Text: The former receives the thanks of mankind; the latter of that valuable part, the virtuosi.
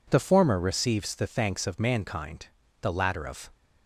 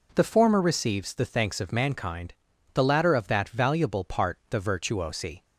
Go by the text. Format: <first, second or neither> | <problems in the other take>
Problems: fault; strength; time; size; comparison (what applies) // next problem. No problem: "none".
second | stops before "that valuable part the virtuosi"; at 3.5 s